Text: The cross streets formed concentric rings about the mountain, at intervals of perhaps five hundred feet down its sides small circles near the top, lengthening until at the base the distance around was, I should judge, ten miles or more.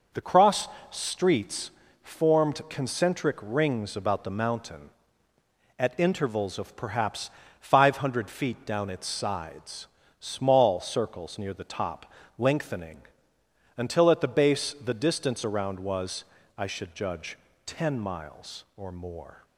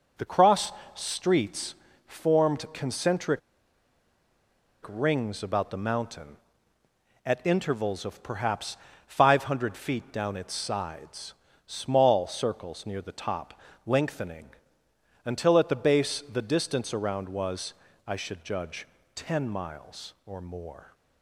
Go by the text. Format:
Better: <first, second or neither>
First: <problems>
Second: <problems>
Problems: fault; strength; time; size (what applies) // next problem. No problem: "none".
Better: first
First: pauses between "cross" and "streets"; slight; at 0.6 s; 0.22 s long // pauses between "streets" and "formed"; slight; at 1.7 s; 0.30 s long // pauses between "perhaps" and "five"; slight; at 7.2 s; 0.30 s long // pauses between "sides" and "small"; slight; at 9.8 s; 0.32 s long // pauses between "lengthening" and "until"; noticeable; at 12.9 s; 0.78 s long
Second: pauses between "cross" and "streets"; slight; at 0.7 s; 0.22 s long // pauses between "streets" and "formed"; slight; at 1.7 s; 0.30 s long // pauses between "concentric" and "rings"; strong; at 3.3 s; 1.4 s long // pauses between "perhaps" and "five"; slight; at 8.7 s; 0.30 s long // pauses between "sides" and "small"; slight; at 11.3 s; 0.32 s long // pauses between "lengthening" and "until"; noticeable; at 14.4 s; 0.78 s long